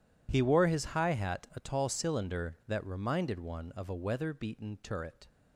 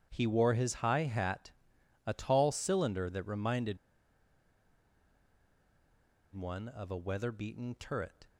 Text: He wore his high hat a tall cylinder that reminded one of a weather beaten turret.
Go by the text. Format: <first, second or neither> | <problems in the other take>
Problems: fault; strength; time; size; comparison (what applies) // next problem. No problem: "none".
first | starts louder than the rest; strong; until 1.1 s; 9.5 dB // pauses between "hat" and "a"; noticeable; at 1.5 s; 0.56 s long // pauses between "reminded" and "one"; strong; at 3.7 s; 2.5 s long